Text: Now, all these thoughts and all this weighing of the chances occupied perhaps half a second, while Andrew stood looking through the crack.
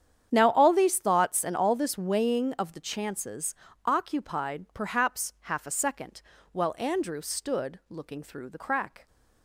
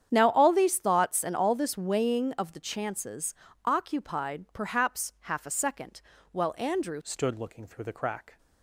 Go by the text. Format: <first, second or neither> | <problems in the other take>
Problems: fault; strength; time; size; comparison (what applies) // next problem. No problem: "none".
first | starts louder than the rest; strong; until 1.1 s; 9 dB; strong in the first // pauses between "chances" and "occupied"; slight; at 3.3 s; 0.30 s long; slight in the first // changes voice at "stood"; from 7.0 s on; 1.3 s long